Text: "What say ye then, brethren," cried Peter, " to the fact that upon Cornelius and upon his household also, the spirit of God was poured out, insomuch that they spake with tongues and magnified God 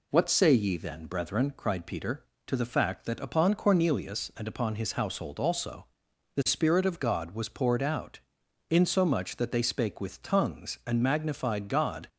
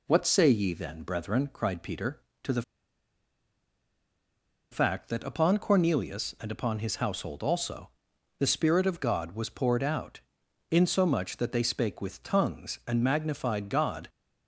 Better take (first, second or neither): first